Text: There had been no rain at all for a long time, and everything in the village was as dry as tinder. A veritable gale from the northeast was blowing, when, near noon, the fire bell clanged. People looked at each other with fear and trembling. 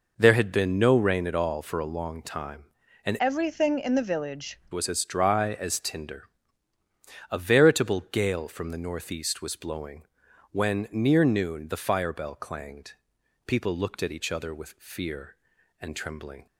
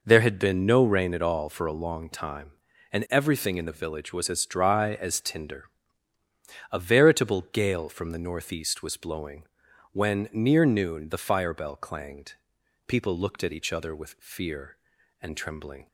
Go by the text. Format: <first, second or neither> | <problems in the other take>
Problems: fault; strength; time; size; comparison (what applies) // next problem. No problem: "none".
second | changes voice from "everything" to "village"; from 3.1 to 4.6 s; 1.5 s long